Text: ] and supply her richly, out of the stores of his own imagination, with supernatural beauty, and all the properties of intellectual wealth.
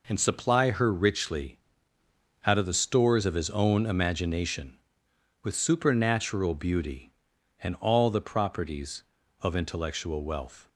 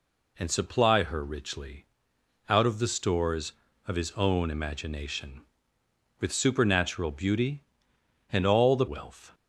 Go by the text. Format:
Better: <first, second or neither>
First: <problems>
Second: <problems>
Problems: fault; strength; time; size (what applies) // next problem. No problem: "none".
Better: first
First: none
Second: skips "properties of intellectual"; at 8.8 s